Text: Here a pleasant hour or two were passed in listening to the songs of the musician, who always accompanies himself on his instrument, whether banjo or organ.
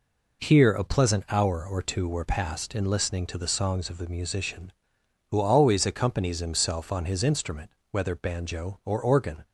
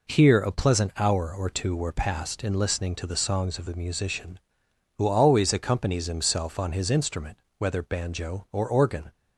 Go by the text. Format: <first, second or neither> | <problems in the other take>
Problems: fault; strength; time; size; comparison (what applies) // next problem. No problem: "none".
neither | none